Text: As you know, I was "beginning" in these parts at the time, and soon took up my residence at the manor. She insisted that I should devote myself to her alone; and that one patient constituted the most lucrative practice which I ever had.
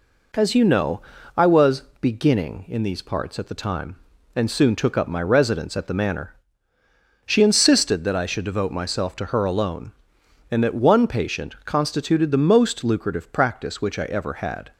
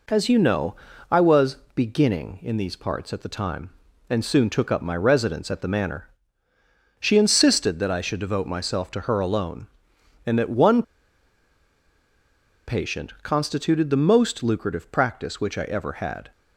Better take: first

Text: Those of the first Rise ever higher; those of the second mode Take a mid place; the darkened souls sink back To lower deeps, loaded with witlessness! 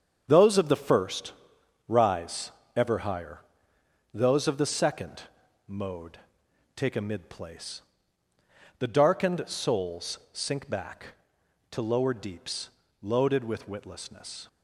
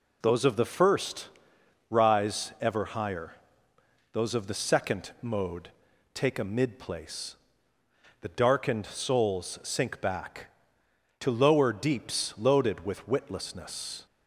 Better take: second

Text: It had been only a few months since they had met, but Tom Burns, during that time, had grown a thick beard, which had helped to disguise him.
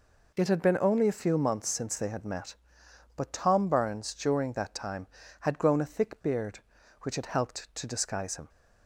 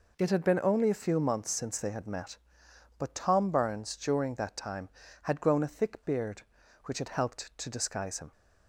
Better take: neither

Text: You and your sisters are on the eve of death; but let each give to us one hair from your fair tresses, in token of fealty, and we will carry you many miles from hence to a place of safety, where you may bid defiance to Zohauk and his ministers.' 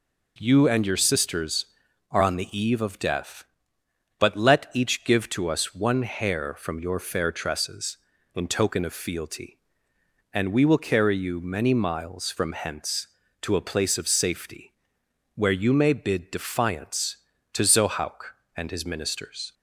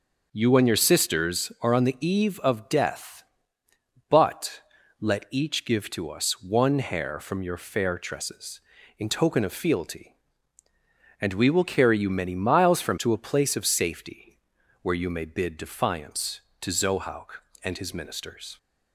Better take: first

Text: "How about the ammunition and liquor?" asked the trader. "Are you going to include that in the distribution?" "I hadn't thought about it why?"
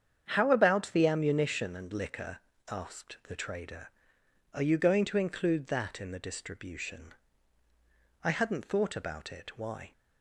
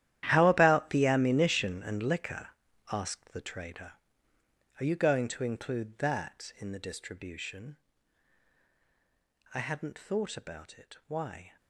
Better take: first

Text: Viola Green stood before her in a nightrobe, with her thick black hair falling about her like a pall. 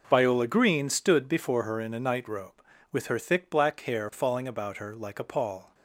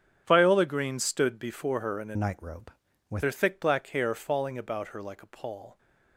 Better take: first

